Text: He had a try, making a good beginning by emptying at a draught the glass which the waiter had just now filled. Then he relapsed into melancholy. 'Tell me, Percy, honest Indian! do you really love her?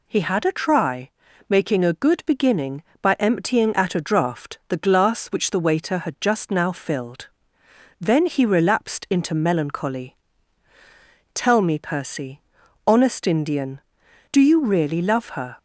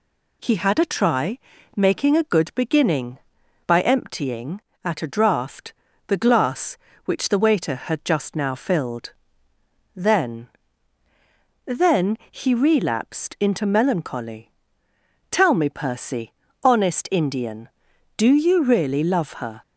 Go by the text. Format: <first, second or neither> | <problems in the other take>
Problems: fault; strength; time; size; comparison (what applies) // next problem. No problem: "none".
first | pauses between "draught" and "the"; slight; at 5.7 s; 0.34 s long // says "Then" twice; at 11.6 s